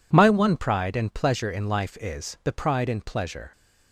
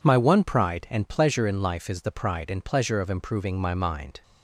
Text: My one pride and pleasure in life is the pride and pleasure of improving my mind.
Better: second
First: stops before "of improving my mind"; at 3.5 s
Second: none

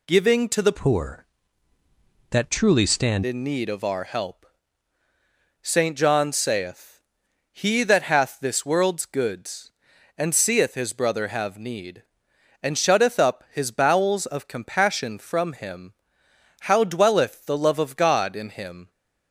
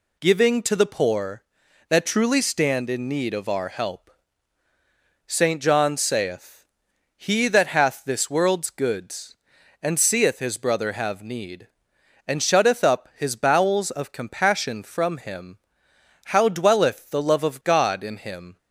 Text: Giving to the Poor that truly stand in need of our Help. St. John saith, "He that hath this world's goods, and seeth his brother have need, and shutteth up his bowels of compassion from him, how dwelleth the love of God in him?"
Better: second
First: changes voice from "Poor" to "stand"; from 0.7 to 3.2 s; 2.5 s long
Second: none

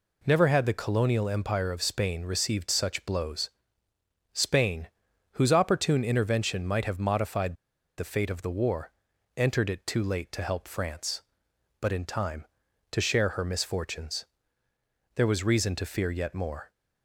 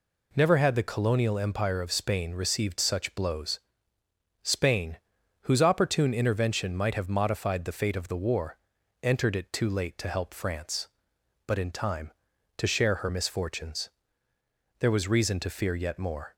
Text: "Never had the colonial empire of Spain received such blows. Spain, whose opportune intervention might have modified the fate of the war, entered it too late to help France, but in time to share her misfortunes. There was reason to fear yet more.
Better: second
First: pauses between "modified" and "the"; at 7.5 s; 0.42 s long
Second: none

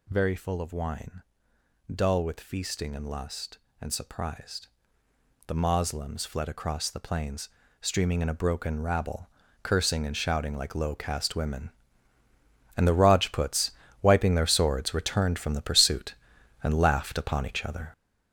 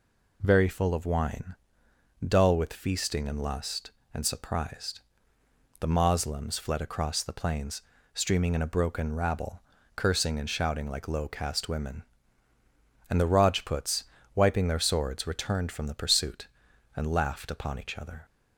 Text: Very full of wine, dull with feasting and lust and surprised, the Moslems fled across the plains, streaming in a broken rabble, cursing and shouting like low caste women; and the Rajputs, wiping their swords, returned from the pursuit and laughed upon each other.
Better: second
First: gets louder; strong; throughout; 7.5 dB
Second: none

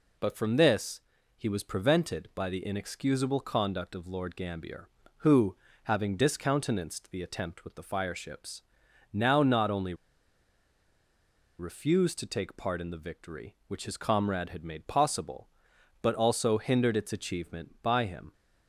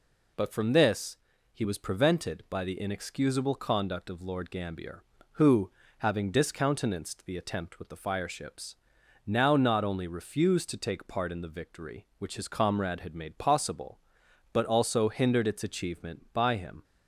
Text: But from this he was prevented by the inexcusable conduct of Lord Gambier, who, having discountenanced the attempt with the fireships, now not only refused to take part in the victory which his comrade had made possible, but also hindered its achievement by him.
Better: second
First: pauses between "this" and "he"; at 0.9 s; 0.40 s long // pauses between "only" and "refused"; strong; at 9.9 s; 1.6 s long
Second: pauses between "this" and "he"; at 1.1 s; 0.40 s long

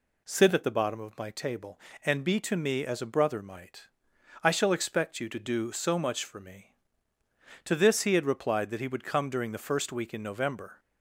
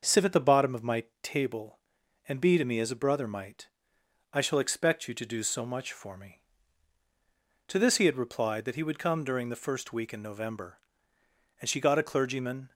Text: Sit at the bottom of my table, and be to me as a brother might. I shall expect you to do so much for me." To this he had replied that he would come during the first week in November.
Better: first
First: none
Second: starts louder than the rest; until 1.2 s; 6 dB // pauses between "my" and "table"; slight; at 1.0 s; 0.18 s long // goes on to say "And she got a clergyman"; noticeable; from 11.6 s on; 1.1 s long

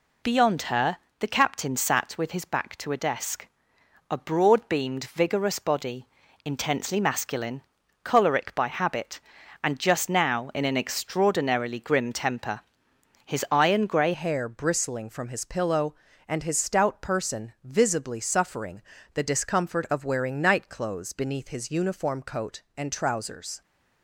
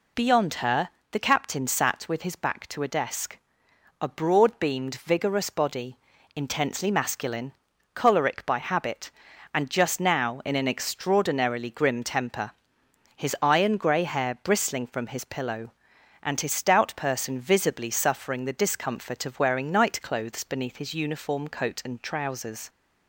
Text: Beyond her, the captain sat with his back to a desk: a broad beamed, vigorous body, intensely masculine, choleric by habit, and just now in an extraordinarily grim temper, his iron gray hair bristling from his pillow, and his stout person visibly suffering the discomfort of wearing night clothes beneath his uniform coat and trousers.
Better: second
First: changes voice at "hair"; from 14.1 s on; 9.5 s long // pauses between "suffering" and "the"; slight; at 18.8 s; 0.32 s long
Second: none

